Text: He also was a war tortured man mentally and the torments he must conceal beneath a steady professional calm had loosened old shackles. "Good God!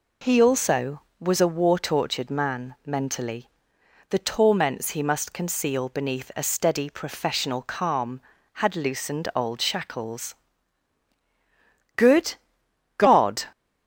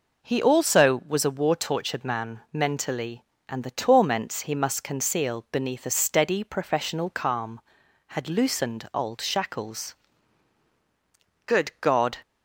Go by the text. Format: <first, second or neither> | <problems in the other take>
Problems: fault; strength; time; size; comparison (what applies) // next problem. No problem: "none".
second | skips "and"; at 3.8 s // pauses between "Good" and "God"; noticeable; at 12.3 s; 0.64 s long